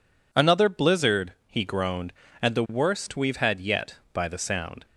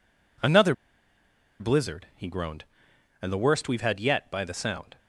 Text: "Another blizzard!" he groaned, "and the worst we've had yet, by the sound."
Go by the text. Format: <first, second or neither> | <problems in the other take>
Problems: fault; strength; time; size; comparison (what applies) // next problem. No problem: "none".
first | pauses between "Another" and "blizzard"; noticeable; at 0.7 s; 0.86 s long